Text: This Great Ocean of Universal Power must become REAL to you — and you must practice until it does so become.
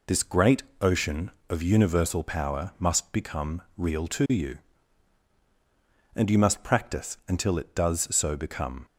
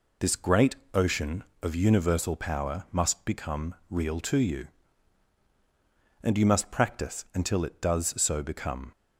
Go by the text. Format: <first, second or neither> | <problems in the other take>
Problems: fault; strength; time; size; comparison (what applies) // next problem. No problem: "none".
neither | pauses between "Great" and "Ocean"; slight; the same in both // pauses between "become" and "REAL"; slight; the same in both